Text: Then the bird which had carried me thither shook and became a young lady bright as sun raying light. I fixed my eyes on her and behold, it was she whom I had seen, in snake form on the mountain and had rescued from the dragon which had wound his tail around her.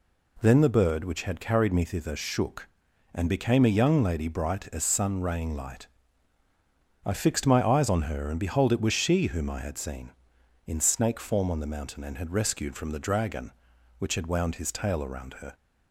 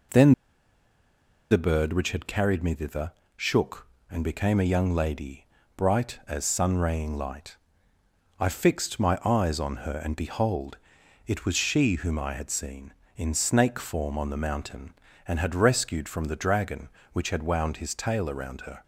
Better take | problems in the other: first | pauses between "Then" and "the"; at 0.3 s; 1.1 s long // pauses between "thither" and "shook"; slight; at 3.1 s; 0.24 s long // pauses between "lady" and "bright"; slight; at 5.4 s; 0.30 s long

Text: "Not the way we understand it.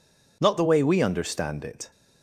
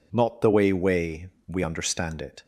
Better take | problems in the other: first | says "way" twice; at 0.7 s

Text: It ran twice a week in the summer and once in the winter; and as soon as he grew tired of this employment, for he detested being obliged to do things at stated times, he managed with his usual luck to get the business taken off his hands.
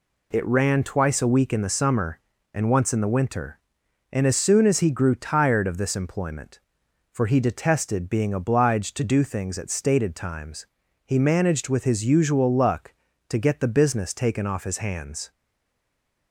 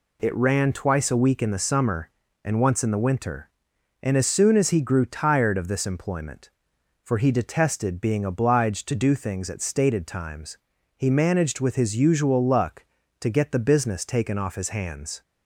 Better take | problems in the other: second | stays silent after the last word; from 15.3 s on; 1.0 s long

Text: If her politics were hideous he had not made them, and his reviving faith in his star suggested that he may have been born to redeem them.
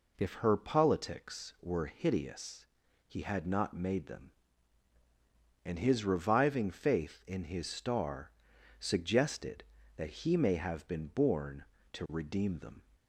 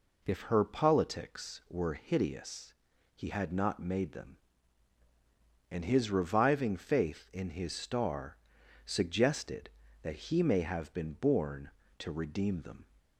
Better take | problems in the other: neither | pauses between "hideous" and "he"; the same in both // pauses between "star" and "suggested"; noticeable; the same in both

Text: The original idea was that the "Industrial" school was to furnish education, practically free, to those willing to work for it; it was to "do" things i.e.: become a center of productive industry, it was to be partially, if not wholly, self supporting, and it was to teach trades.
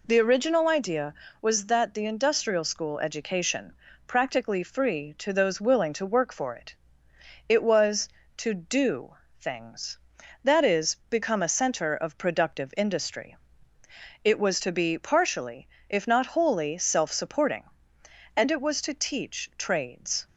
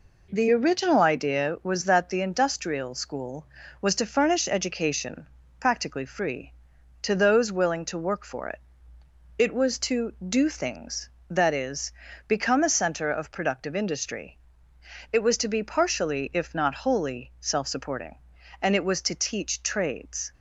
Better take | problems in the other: second | skips "was to furnish"; at 2.9 s // pauses between "do" and "things"; slight; at 9.1 s; 0.24 s long

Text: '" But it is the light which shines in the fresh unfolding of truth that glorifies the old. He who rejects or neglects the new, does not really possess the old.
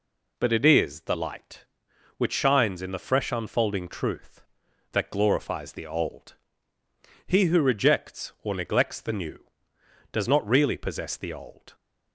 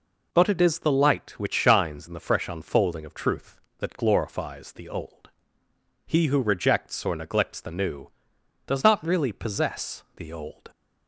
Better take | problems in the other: second | skips "of"; at 3.8 s

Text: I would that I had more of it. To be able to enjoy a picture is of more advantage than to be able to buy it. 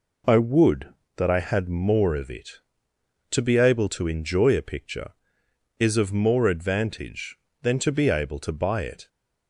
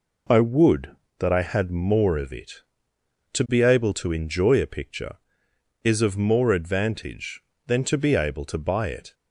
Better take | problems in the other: neither | none

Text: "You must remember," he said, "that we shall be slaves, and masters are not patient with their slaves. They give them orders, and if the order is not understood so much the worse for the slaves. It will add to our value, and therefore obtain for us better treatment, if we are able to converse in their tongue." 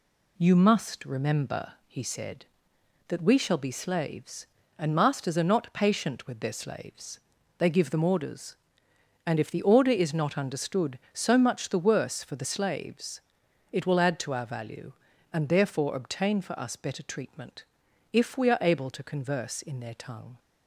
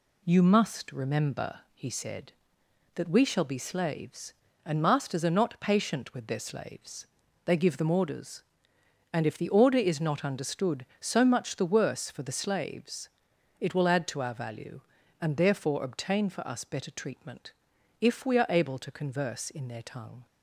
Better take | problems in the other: neither | none

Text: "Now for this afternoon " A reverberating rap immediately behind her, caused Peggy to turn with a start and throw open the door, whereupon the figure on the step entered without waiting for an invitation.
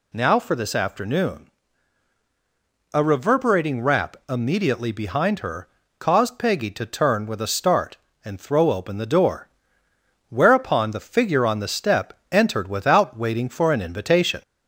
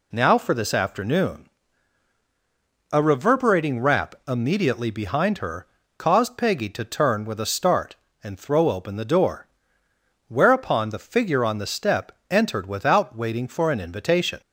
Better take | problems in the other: second | gets louder; strong; throughout; 10 dB // pauses between "step" and "entered"; slight; at 12.1 s; 0.18 s long; slight in the second

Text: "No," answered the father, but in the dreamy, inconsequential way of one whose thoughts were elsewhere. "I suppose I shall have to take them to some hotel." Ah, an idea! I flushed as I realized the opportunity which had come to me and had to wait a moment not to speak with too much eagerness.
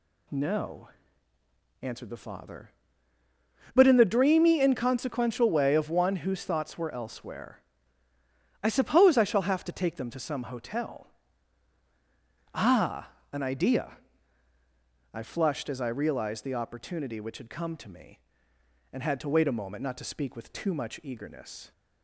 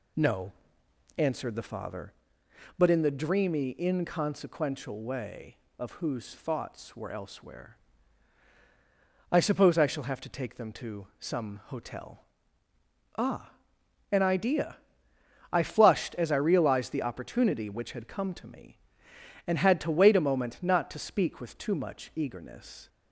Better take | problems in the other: first | skips "one"; at 5.9 s

